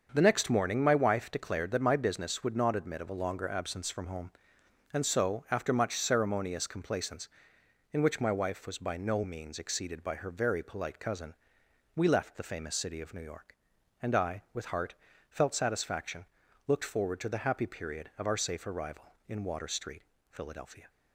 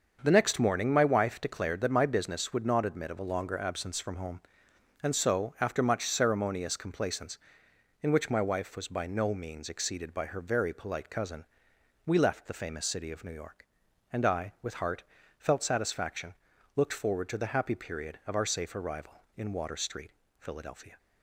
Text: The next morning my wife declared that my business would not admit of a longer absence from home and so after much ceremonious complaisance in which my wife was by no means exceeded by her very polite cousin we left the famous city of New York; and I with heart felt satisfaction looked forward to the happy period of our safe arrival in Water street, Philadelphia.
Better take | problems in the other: neither | starts louder than the rest; the same in both // pauses between "cousin" and "we"; noticeable; the same in both // pauses between "heart" and "felt"; slight; the same in both // pauses between "satisfaction" and "looked"; the same in both

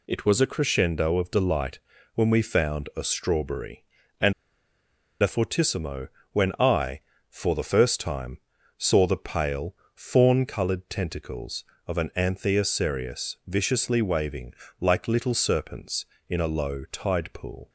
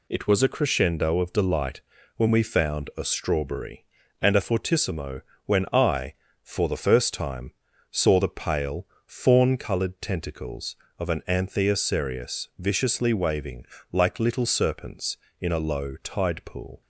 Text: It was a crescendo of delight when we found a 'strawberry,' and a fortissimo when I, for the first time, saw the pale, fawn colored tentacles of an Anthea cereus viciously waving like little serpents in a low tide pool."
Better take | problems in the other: second | pauses between "delight" and "when"; slight; at 1.7 s; 0.36 s long; slight in the second // pauses between "and" and "a"; noticeable; at 4.3 s; 0.88 s long // pauses between "fortissimo" and "when"; slight; at 6.0 s; 0.24 s long; slight in the second // pauses between "waving" and "like"; slight; at 14.5 s; 0.26 s long; slight in the second

